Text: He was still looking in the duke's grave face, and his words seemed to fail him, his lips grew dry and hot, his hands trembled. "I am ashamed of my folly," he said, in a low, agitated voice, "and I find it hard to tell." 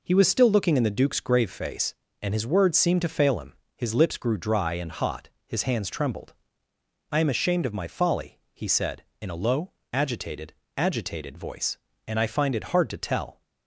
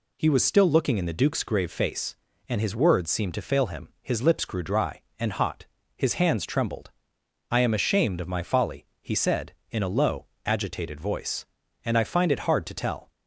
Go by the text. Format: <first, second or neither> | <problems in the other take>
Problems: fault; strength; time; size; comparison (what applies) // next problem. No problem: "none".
second | says "agitated" twice; at 10.7 s